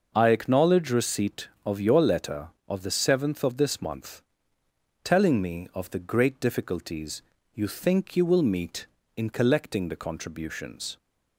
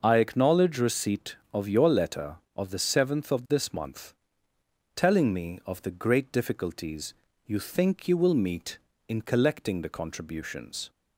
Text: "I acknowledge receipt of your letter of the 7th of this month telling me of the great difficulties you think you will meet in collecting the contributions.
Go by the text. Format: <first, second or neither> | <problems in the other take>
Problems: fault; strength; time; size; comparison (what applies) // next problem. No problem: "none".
neither | starts louder than the rest; noticeable; the same in both // pauses between "month" and "telling"; noticeable; the same in both // pauses between "difficulties" and "you"; slight; the same in both